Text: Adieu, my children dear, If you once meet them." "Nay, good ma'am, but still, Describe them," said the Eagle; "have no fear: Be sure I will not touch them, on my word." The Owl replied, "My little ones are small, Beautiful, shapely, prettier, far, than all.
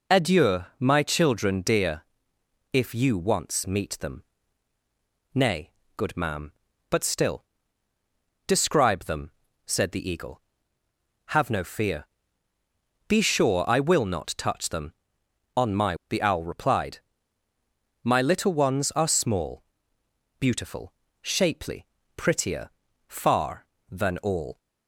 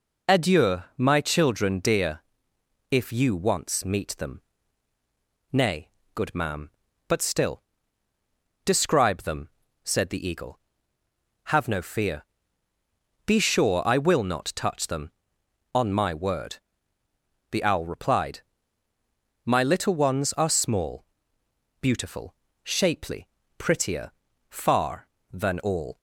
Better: second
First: skips "word"; at 16.0 s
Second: none

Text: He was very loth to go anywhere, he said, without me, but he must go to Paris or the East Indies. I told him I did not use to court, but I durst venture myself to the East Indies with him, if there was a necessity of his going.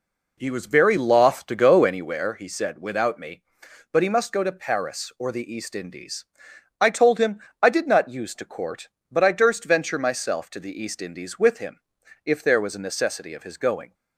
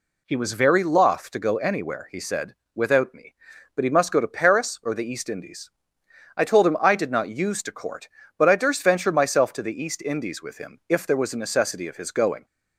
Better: second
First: starts louder than the rest; until 2.1 s; 3.5 dB // pauses between "him" and "I"; slight; at 7.3 s; 0.20 s long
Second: none

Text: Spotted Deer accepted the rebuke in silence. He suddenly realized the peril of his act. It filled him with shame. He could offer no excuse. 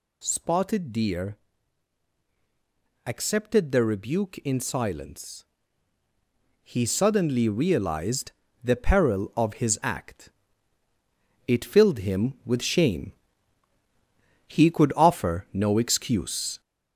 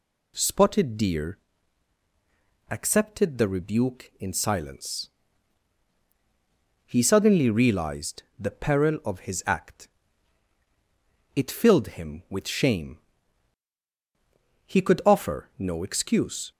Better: second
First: gets louder; noticeable; throughout; 4.5 dB // pauses between "Deer" and "accepted"; strong; at 1.3 s; 1.7 s long // pauses between "realized" and "the"; slight; at 8.3 s; 0.32 s long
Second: pauses between "Deer" and "accepted"; strong; at 1.3 s; 1.3 s long

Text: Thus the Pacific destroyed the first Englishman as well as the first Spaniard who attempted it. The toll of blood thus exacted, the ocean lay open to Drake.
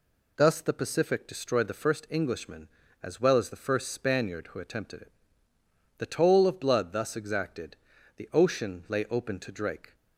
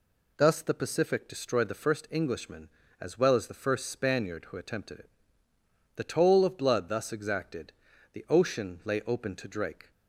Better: neither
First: none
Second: none

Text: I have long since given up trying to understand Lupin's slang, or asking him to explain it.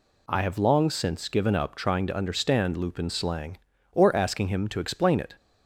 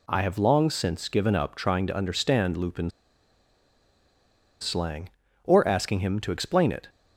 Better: first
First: none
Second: pauses between "Lupin's" and "slang"; strong; at 2.9 s; 1.7 s long

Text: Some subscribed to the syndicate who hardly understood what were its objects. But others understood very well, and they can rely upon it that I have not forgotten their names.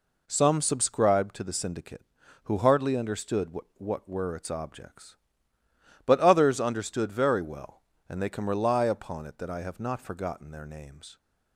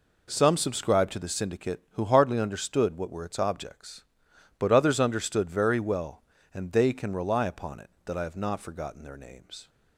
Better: second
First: says "what" twice; at 3.7 s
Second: none

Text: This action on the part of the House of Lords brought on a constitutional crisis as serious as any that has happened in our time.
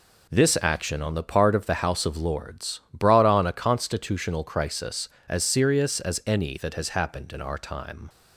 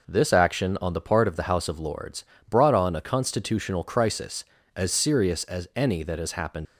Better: first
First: none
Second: pauses between "Lords" and "brought"; slight; at 2.2 s; 0.24 s long // stops before "in our time"; at 6.6 s

